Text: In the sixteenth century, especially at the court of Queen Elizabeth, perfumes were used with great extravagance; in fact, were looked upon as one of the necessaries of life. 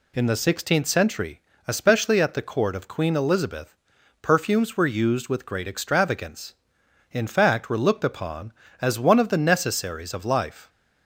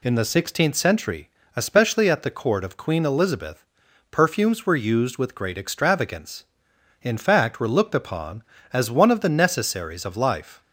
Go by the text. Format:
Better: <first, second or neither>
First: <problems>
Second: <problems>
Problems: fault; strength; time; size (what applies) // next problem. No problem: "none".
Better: neither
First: none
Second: none